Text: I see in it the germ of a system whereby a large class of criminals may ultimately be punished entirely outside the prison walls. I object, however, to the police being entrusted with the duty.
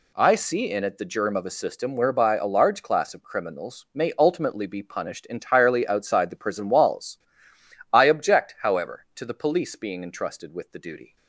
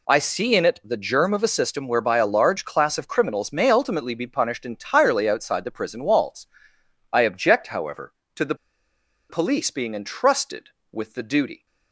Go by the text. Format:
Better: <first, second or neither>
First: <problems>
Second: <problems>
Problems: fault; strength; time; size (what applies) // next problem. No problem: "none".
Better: first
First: none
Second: pauses between "the" and "police"; noticeable; at 8.5 s; 0.74 s long